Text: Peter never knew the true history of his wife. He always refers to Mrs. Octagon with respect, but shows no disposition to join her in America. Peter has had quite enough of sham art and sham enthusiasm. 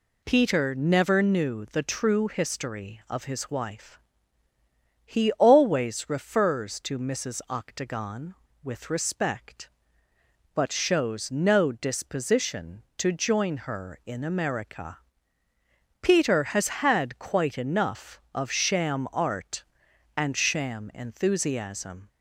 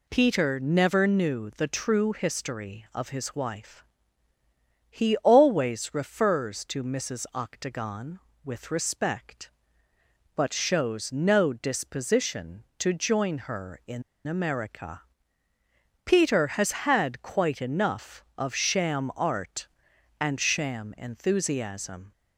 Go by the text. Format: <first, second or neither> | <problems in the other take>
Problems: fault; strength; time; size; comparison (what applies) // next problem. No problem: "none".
first | pauses between "in" and "America"; slight; at 14.0 s; 0.25 s long